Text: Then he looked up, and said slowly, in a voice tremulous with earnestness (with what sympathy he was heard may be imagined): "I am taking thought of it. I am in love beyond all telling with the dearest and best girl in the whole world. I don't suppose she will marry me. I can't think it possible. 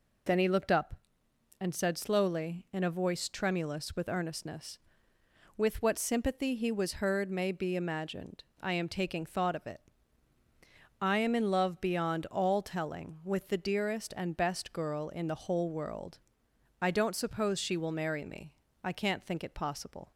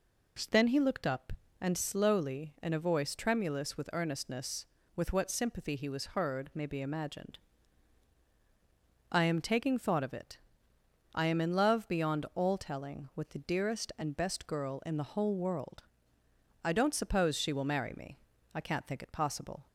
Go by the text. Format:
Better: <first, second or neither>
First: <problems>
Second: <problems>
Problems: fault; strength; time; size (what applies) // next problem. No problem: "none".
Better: first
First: none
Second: skips "said"; at 1.7 s